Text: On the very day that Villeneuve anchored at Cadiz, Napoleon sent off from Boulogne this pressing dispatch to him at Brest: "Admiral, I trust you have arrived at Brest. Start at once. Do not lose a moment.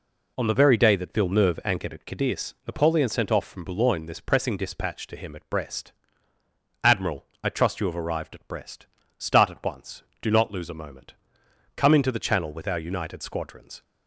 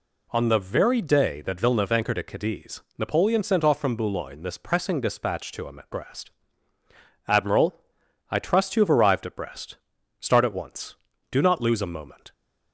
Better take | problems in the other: second | goes on to say "Come into the Channel with our united squadrons"; strong; from 11.7 s on; 2.0 s long

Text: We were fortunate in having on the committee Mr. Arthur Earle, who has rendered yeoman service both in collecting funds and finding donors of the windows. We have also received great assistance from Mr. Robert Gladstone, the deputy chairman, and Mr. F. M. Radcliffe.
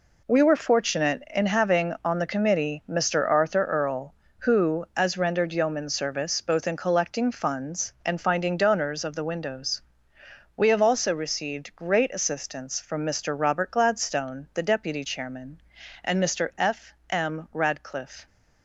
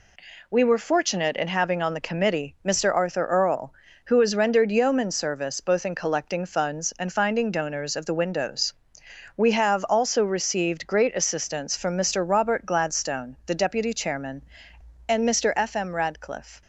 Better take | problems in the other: second | says "as" for "has"; at 4.9 s // pauses between "F" and "M"; slight; at 16.9 s; 0.16 s long

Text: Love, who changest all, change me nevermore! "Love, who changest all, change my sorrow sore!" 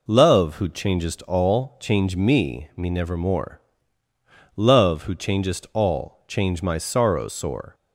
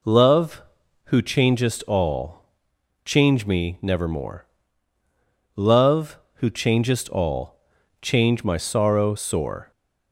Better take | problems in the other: second | says "me" twice; at 2.7 s

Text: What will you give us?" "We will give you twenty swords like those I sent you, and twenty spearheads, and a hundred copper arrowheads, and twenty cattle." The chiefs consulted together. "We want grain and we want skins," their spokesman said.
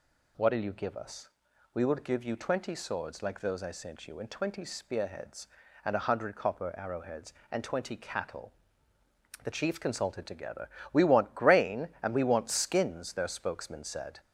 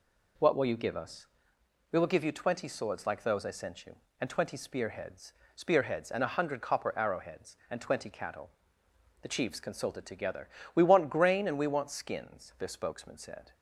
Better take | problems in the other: first | says "spearheads" twice; at 5.5 s

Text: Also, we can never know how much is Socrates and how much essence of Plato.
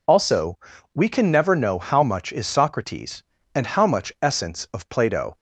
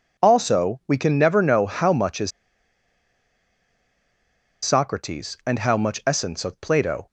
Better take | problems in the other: first | pauses between "is" and "Socrates"; strong; at 2.3 s; 2.3 s long

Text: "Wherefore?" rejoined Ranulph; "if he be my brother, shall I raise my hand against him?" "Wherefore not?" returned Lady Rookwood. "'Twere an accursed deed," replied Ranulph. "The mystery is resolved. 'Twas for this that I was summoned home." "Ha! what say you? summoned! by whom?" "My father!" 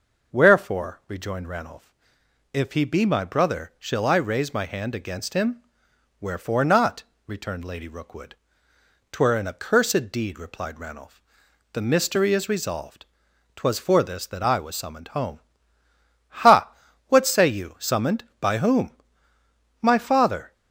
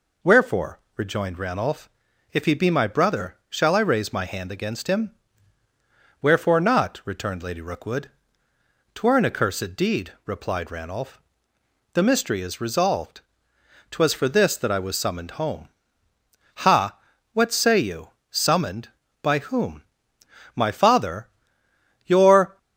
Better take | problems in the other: first | goes on to say "Your"; from 22.0 s on; 0.50 s long

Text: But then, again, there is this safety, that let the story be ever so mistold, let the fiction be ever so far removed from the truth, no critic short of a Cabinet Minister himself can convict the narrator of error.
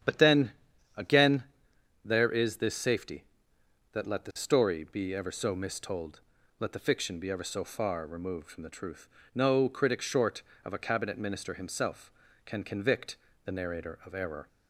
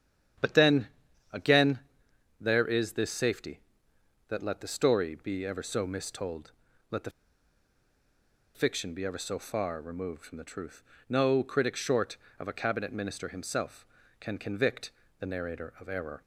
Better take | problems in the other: first | starts louder than the rest; strong; until 2.4 s; 9 dB; strong in the first // pauses between "the" and "fiction"; strong; at 7.1 s; 1.4 s long // pauses between "convict" and "the"; slight; at 14.9 s; 0.26 s long; slight in the first

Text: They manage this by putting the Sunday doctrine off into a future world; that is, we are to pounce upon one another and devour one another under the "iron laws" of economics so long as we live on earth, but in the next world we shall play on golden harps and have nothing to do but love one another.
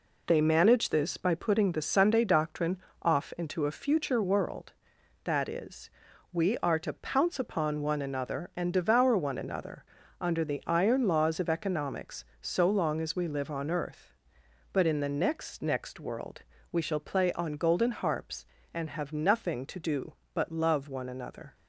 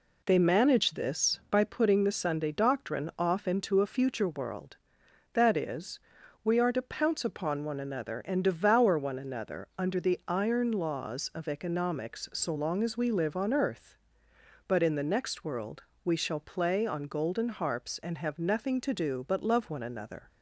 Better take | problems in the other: second | pauses between "doctrine" and "off"; slight; at 2.7 s; 0.24 s long // pauses between "another" and "under"; at 9.8 s; 0.38 s long // says "next" twice; at 15.6 s // pauses between "world" and "we"; slight; at 16.4 s; 0.32 s long; slight in the second

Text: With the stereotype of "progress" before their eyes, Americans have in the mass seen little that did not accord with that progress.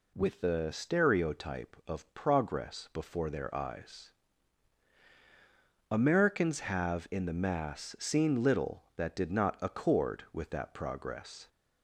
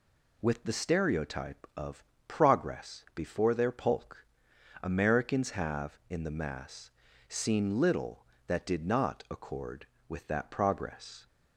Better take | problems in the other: first | pauses between "of" and "progress"; slight; at 2.0 s; 0.24 s long // says "polk" for "eyes"; at 3.7 s // pauses between "mass" and "seen"; slight; at 6.9 s; 0.36 s long

